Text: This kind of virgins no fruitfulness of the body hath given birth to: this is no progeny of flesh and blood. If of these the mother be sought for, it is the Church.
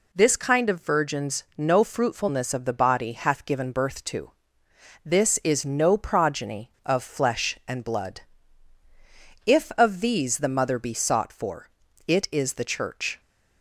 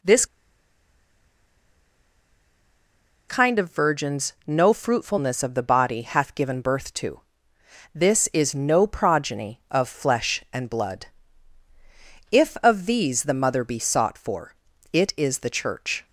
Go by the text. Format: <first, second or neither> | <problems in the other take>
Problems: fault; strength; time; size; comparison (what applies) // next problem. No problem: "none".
first | pauses between "This" and "kind"; strong; at 0.2 s; 3.0 s long